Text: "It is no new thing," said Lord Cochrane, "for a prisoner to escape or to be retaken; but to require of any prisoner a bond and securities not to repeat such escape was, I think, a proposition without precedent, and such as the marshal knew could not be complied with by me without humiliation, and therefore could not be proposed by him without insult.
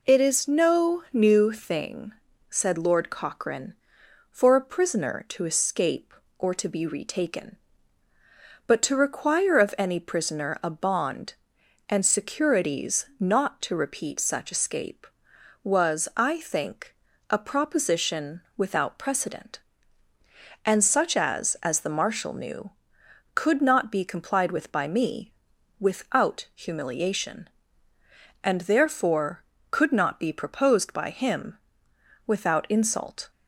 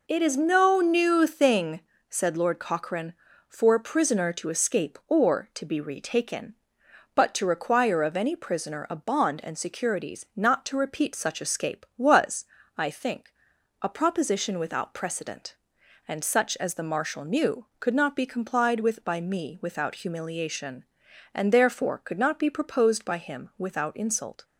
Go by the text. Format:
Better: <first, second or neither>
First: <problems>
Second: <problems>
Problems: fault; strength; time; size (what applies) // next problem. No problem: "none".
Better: second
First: pauses between "proposition" and "without"; slight; at 18.4 s; 0.16 s long // says "as" twice; at 21.6 s // pauses between "me" and "without"; noticeable; at 25.3 s; 0.46 s long // pauses between "him" and "without"; noticeable; at 31.5 s; 0.70 s long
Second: none